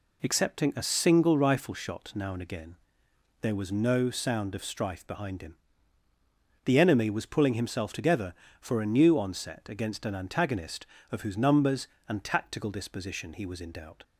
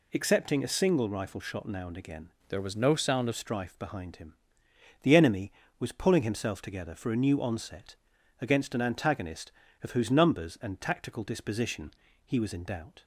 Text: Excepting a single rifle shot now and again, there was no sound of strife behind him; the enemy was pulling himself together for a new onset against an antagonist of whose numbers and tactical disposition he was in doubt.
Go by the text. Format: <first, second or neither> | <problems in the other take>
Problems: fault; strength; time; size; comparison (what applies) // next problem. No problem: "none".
first | changes voice from "there" to "of"; from 2.5 to 3.3 s; 0.8 s long // pauses between "onset" and "against"; at 7.9 s; 0.44 s long // pauses between "disposition" and "he"; slight; at 11.9 s; 0.32 s long